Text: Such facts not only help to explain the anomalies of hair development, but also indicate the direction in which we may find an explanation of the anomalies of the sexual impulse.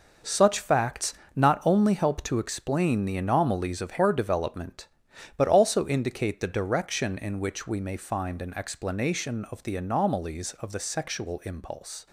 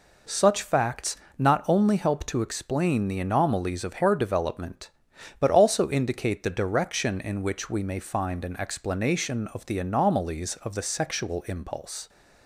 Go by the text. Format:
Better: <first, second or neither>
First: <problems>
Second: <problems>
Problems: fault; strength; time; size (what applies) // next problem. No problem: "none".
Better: second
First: gets quieter; strong; throughout; 9 dB // pauses between "facts" and "not"; slight; at 1.1 s; 0.24 s long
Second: pauses between "facts" and "not"; slight; at 1.1 s; 0.24 s long